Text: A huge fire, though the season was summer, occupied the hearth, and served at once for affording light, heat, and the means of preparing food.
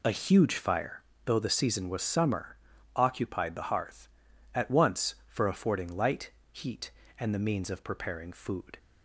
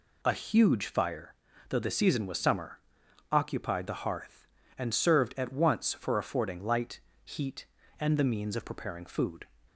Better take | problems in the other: second | skips "and served"; at 4.3 s

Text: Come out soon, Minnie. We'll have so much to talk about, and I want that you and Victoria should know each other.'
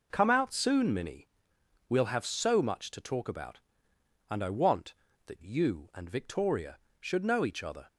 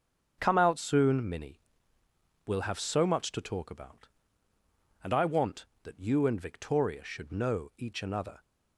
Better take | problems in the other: first | starts louder than the rest; until 1.3 s; 7 dB // says "another" for "other"; at 8.0 s

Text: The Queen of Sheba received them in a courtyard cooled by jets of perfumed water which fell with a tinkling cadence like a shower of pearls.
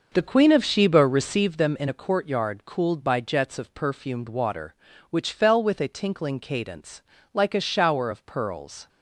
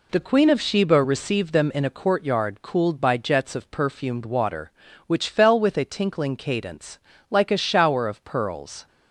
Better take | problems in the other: second | starts louder than the rest; noticeable; until 1.6 s; 6 dB // pauses between "cadence" and "like"; slight; at 7.0 s; 0.28 s long; slight in the second

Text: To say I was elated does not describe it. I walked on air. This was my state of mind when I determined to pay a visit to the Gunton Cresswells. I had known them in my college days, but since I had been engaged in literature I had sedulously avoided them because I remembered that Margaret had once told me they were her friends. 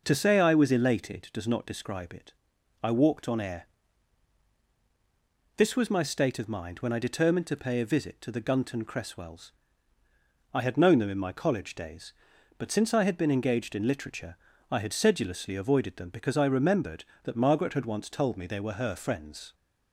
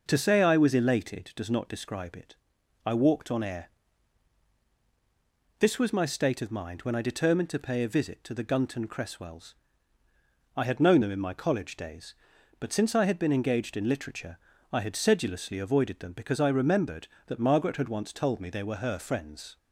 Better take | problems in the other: neither | pauses between "literature" and "I"; slight; the same in both

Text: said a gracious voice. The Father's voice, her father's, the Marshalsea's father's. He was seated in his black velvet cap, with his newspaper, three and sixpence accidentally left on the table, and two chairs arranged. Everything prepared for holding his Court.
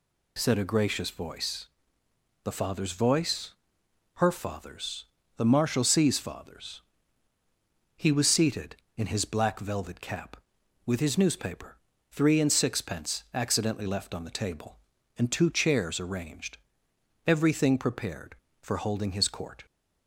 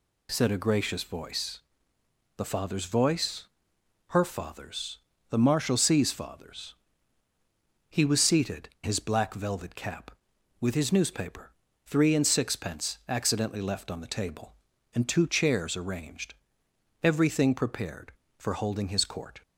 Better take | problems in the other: first | skips "in"; at 8.7 s

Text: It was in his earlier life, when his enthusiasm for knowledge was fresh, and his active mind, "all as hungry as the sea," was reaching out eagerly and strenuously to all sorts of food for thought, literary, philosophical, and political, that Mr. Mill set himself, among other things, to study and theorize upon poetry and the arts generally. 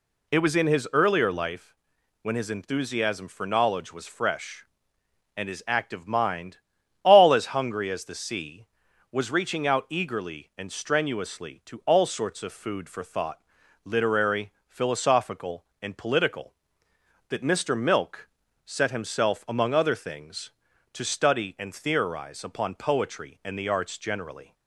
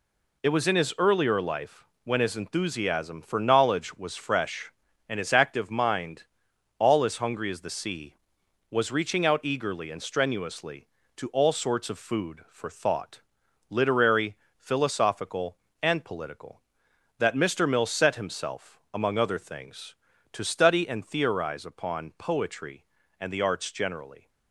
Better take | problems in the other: second | says "Milk" for "Mill"; at 17.7 s

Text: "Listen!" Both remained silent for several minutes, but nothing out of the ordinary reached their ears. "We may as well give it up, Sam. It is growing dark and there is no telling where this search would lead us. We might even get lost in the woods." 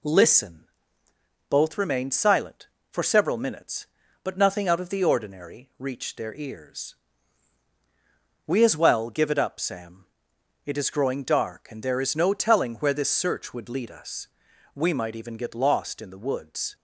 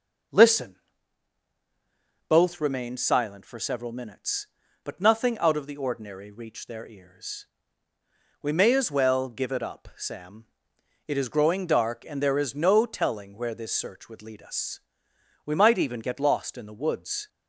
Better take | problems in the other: second | skips "may"; at 8.6 s

